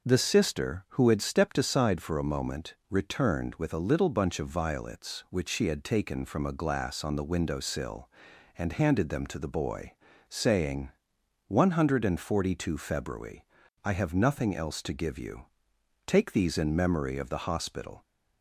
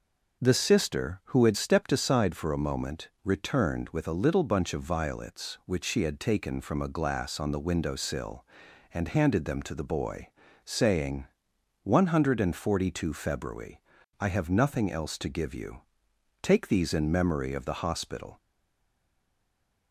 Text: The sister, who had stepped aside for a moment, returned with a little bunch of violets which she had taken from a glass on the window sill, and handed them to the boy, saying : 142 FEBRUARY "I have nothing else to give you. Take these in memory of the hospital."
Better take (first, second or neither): first